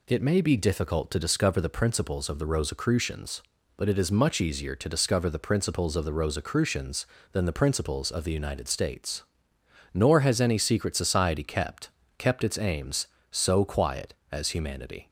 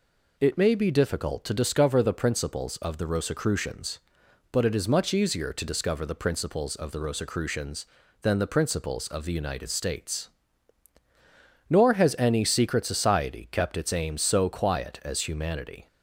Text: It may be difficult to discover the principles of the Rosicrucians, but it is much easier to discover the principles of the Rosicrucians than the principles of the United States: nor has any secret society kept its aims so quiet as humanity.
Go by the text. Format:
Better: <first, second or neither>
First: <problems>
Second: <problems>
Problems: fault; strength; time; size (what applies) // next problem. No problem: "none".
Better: second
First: says "kept" twice; at 12.1 s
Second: none